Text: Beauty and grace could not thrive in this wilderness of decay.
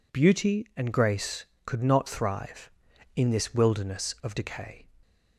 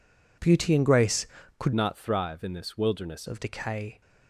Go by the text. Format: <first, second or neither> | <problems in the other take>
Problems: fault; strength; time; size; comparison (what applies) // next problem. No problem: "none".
first | changes voice from "not" to "wilderness"; from 1.7 to 3.2 s; 1.5 s long